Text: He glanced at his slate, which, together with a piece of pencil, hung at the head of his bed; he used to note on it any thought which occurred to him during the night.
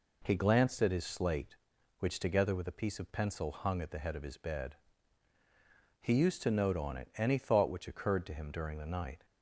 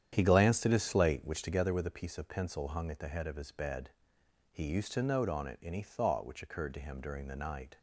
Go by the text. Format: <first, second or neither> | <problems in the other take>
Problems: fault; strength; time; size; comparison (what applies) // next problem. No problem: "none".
first | starts louder than the rest; strong; until 1.7 s; 9.5 dB